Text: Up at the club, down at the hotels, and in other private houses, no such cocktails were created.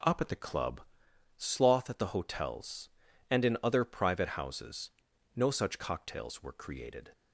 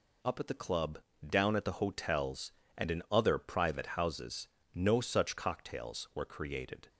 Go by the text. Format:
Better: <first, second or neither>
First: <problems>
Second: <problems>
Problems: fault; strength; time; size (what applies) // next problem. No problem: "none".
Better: second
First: says "sloth" for "down"; at 1.3 s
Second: none